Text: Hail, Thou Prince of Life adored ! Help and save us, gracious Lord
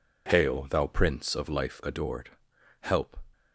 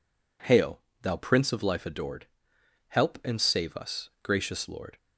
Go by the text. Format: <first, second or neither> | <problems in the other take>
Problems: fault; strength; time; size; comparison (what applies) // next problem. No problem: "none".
second | stops before "and save us gracious Lord"; at 3.3 s